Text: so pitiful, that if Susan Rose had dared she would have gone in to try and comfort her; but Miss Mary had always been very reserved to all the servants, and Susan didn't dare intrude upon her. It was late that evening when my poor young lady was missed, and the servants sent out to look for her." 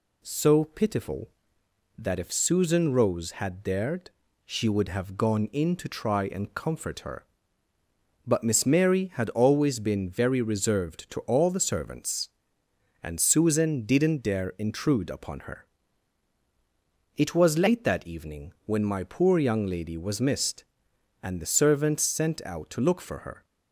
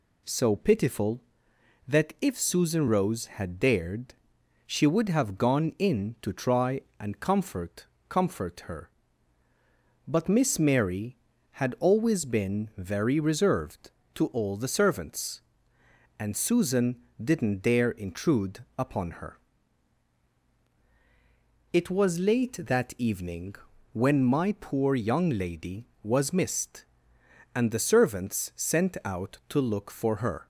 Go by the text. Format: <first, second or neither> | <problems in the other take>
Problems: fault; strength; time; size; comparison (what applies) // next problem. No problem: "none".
first | pauses between "dared" and "she"; noticeable; at 4.1 s; 0.52 s long; slight in the first // says "comfort" twice; at 8.0 s // pauses between "Susan" and "didn't"; slight; at 16.9 s; 0.26 s long // pauses between "evening" and "when"; slight; at 23.5 s; 0.34 s long